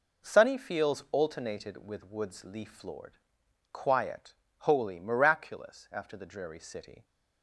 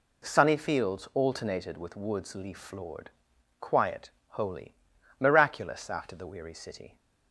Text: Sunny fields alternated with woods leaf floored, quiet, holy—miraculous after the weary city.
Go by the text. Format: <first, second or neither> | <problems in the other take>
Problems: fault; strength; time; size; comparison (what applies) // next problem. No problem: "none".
second | says "dreary" for "weary"; at 6.2 s